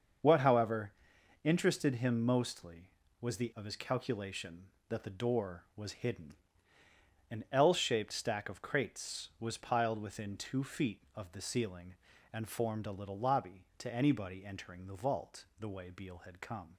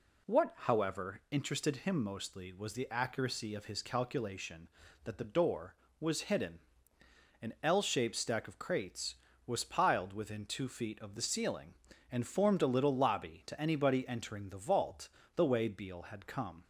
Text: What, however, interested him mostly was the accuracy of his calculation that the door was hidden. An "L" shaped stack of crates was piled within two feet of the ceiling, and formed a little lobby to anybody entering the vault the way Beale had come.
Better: second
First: starts louder than the rest; until 1.7 s; 6.5 dB // skips "accuracy"; at 3.5 s // pauses between "vault" and "the"; slight; at 15.4 s; 0.16 s long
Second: pauses between "vault" and "the"; slight; at 15.0 s; 0.26 s long

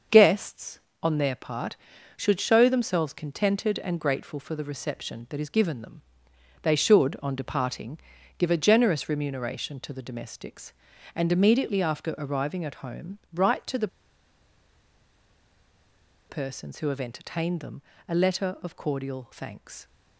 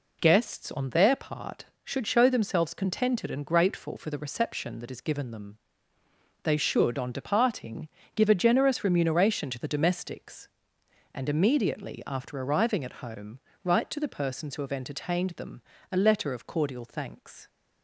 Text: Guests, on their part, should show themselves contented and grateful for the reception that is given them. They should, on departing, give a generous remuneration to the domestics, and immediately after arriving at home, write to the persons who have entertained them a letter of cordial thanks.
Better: second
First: starts louder than the rest; until 1.3 s; 6 dB // pauses between "the" and "persons"; strong; at 13.8 s; 2.4 s long // pauses between "them" and "a"; slight; at 17.8 s; 0.26 s long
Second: pauses between "them" and "a"; slight; at 15.6 s; 0.30 s long

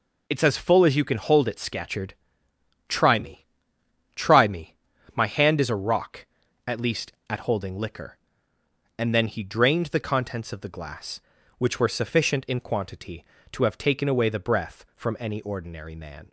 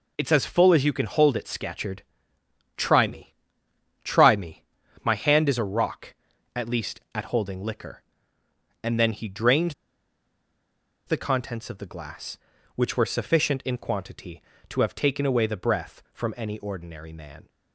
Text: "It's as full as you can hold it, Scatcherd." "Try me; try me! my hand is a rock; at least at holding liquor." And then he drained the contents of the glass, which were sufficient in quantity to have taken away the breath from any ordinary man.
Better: first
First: none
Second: pauses between "drained" and "the"; strong; at 9.7 s; 1.3 s long

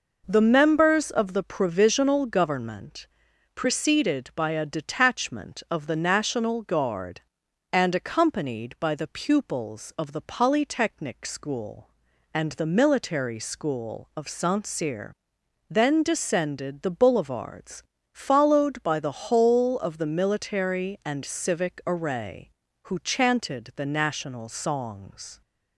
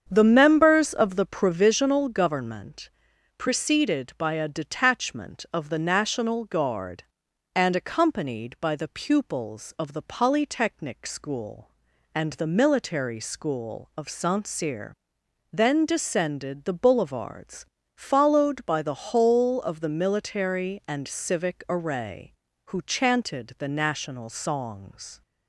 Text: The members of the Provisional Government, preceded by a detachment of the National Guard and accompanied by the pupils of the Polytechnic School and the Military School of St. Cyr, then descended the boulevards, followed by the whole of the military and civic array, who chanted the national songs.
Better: first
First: none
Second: starts louder than the rest; strong; until 1.7 s; 7.5 dB

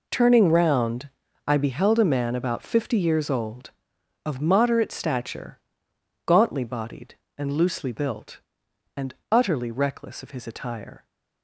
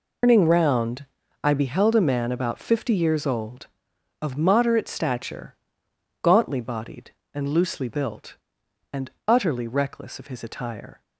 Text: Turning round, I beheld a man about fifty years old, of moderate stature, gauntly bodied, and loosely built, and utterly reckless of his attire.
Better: first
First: pauses between "and" and "utterly"; slight; at 9.1 s; 0.16 s long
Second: loses the start of "Turning"; at 0.2 s; 175 ms // pauses between "and" and "utterly"; slight; at 9.0 s; 0.16 s long

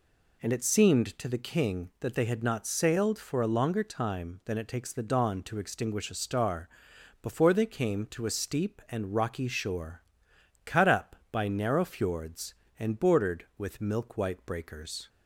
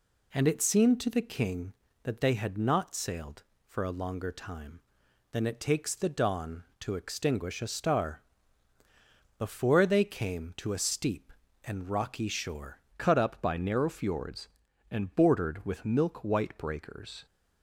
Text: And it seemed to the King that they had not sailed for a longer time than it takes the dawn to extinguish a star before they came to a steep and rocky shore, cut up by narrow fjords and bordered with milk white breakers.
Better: first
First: pauses between "star" and "before"; noticeable; at 6.6 s; 0.54 s long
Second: pauses between "star" and "before"; at 8.2 s; 1.1 s long // changes voice at "cut"; from 12.9 s on; 4.3 s long

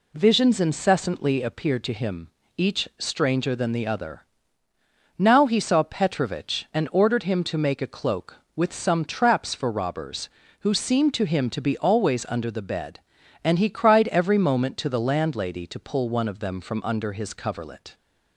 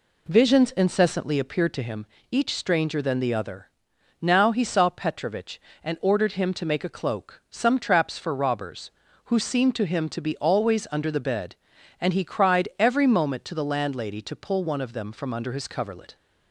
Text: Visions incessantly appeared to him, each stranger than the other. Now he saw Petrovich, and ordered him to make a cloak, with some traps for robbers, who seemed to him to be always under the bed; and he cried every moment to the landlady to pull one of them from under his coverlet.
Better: first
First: none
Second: skips "with"; at 7.4 s

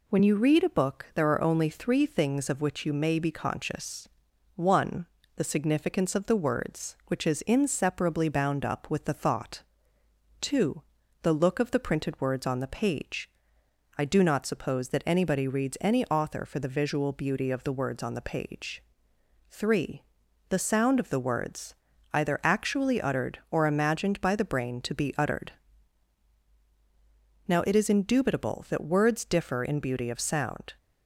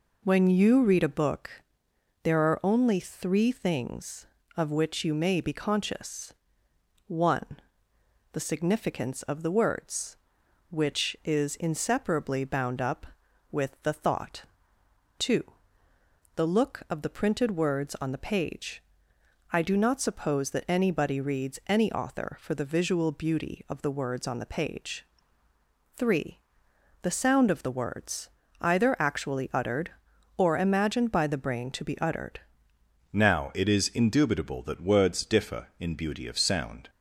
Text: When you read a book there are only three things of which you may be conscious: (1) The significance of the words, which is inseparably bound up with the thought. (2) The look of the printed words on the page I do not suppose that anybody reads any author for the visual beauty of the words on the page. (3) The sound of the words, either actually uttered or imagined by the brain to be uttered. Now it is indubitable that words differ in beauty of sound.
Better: first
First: pauses between "page" and "I"; noticeable; at 13.2 s; 0.68 s long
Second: pauses between "book" and "there"; noticeable; at 1.5 s; 0.72 s long // pauses between "page" and "I"; noticeable; at 18.8 s; 0.70 s long // changes voice at "Now"; from 33.1 s on; 3.7 s long

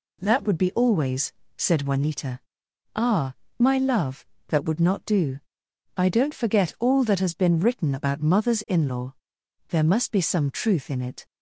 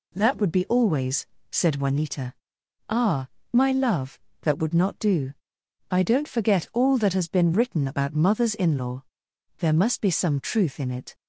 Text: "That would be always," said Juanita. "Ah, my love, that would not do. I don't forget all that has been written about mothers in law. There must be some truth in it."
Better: neither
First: none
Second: none

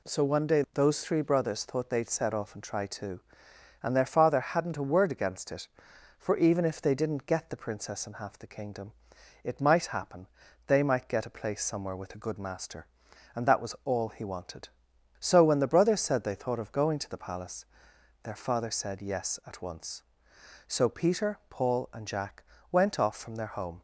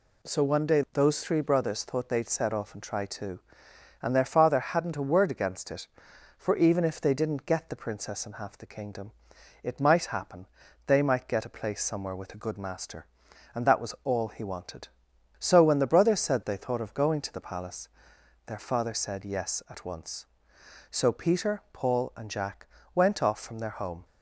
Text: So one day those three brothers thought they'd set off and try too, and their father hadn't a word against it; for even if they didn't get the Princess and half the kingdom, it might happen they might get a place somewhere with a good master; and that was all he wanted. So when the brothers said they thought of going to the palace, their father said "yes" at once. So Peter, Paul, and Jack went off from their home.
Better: neither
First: pauses between "happen" and "they"; at 10.2 s; 0.40 s long // pauses between "Jack" and "went"; slight; at 22.4 s; 0.30 s long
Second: pauses between "happen" and "they"; at 10.4 s; 0.40 s long // pauses between "Jack" and "went"; slight; at 22.6 s; 0.30 s long

